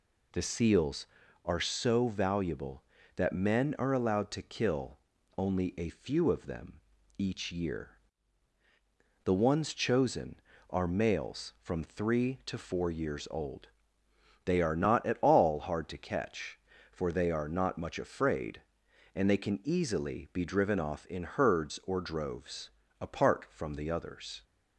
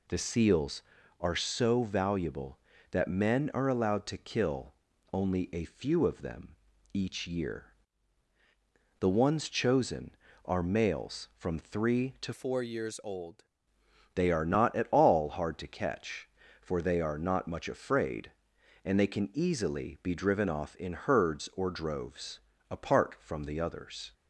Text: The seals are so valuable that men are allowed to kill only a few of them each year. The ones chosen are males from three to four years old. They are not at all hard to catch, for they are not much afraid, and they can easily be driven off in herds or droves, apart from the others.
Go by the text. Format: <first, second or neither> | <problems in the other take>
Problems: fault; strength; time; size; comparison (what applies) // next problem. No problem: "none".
first | pauses between "kill" and "only"; at 4.7 s; 0.40 s long; also in the first // pauses between "them" and "each"; at 6.5 s; 0.38 s long; also in the first // changes voice from "four" to "old"; from 12.3 to 13.4 s; 1.1 s long